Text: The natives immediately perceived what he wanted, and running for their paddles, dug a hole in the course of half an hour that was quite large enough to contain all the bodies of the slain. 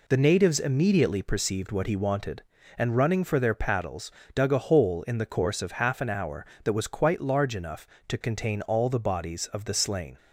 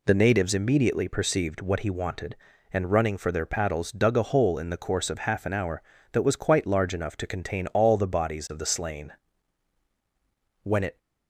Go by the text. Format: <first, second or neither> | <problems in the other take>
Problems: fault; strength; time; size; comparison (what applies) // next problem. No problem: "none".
first | goes on to say "When it"; slight; from 10.6 s on; 0.34 s long